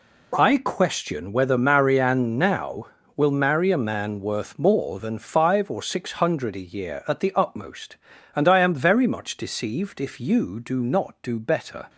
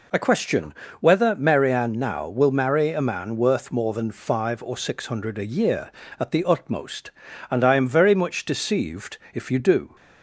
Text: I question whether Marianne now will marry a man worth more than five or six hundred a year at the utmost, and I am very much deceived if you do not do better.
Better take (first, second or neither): first